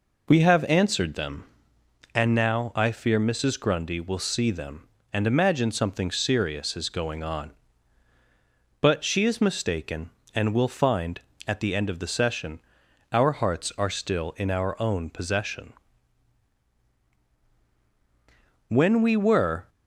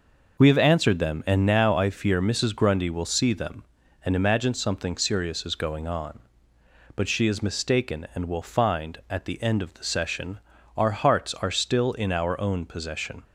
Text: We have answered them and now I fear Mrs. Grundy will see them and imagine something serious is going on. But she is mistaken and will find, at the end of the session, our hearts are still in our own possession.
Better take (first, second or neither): second